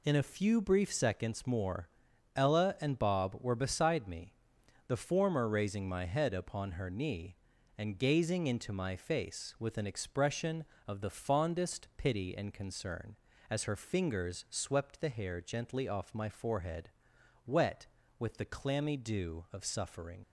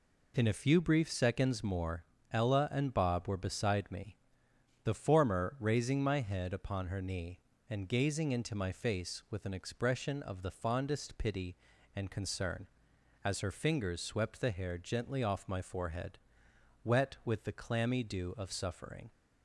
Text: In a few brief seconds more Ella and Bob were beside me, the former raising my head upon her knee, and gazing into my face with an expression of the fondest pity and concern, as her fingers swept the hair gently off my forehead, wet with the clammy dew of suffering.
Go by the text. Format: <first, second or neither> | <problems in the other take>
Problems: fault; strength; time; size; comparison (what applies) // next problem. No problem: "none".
second | pauses between "more" and "Ella"; noticeable; at 1.8 s; 0.48 s long; slight in the second // leaves "suffering" unfinished; at 20.2 s; 45 ms